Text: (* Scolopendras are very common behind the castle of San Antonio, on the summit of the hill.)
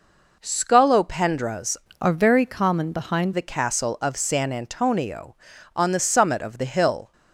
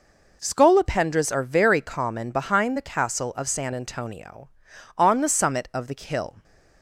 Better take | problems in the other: second | changes voice from "are" to "behind"; from 1.9 to 3.3 s; 1.4 s long

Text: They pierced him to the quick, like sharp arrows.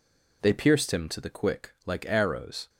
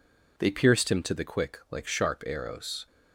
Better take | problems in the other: second | skips "sharp"; at 2.0 s

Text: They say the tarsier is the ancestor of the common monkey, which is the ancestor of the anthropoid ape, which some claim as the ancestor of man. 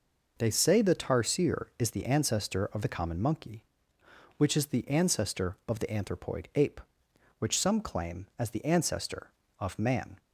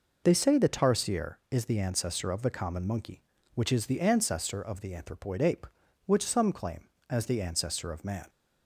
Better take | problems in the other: neither | none

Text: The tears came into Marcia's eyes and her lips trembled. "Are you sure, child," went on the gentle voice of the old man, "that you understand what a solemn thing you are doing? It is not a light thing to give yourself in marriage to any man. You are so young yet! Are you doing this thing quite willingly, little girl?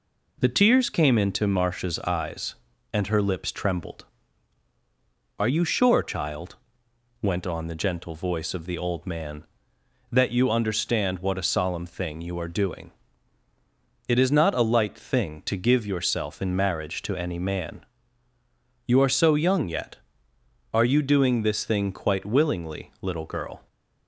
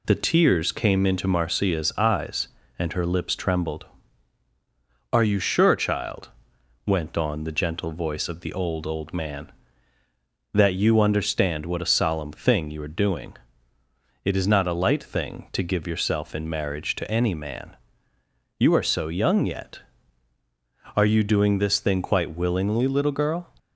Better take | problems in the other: first | says "old" twice; at 8.8 s

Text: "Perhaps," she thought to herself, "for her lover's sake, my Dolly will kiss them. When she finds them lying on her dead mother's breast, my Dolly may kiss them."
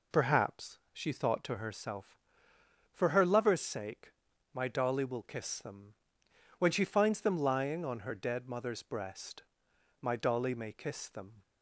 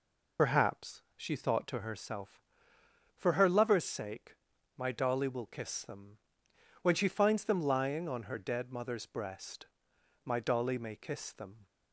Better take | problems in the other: first | loses the start of "Perhaps"; at 0.3 s; 45 ms

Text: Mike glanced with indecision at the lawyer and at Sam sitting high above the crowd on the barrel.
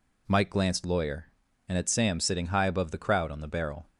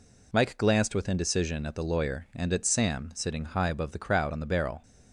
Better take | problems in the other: second | skips "with indecision at the"; at 0.8 s

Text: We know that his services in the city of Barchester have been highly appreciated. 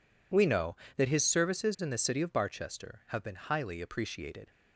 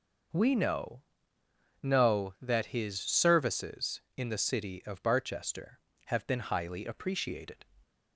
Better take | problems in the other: first | says "know" twice; at 1.8 s

